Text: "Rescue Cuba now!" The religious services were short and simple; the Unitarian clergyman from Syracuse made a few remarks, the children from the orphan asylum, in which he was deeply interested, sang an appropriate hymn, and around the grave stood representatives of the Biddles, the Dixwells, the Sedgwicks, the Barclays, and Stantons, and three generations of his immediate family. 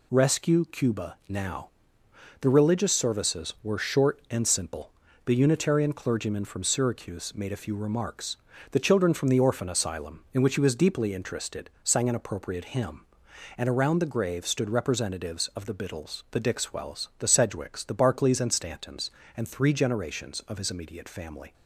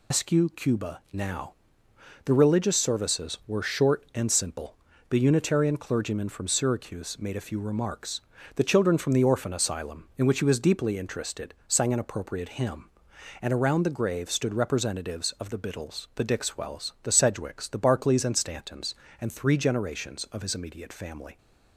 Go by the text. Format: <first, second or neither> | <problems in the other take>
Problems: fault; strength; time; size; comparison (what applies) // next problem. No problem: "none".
first | loses the start of "Rescue"; at 0.1 s; 150 ms